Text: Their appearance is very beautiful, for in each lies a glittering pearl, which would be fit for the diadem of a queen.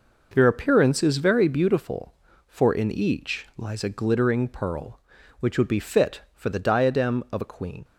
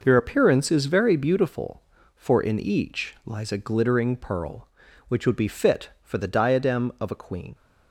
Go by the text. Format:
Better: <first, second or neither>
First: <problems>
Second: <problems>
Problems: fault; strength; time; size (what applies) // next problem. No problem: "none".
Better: neither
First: none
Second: none